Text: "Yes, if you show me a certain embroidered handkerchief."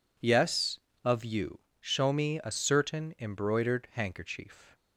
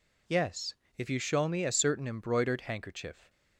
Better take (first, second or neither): second